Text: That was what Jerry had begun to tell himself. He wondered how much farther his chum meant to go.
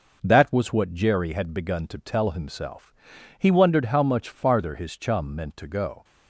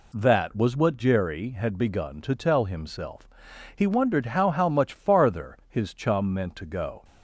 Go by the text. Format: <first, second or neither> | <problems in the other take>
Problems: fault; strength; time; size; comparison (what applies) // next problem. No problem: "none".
first | says "how" twice; at 4.4 s